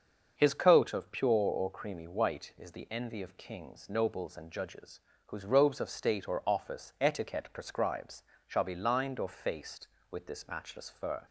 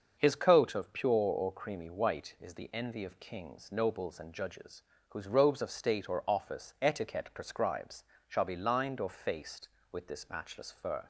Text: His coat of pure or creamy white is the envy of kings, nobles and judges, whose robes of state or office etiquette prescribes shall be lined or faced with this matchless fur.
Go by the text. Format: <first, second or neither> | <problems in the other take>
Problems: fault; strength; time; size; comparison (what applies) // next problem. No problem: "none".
neither | starts louder than the rest; the same in both // pauses between "prescribes" and "shall"; slight; the same in both